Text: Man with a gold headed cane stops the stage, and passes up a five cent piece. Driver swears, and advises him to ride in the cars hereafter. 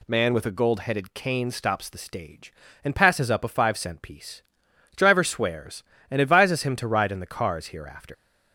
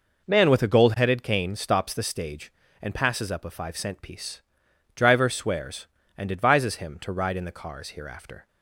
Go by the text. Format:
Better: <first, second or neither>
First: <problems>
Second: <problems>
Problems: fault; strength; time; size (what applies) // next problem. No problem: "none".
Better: second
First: leaves "hereafter" unfinished; at 8.1 s; 125 ms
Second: none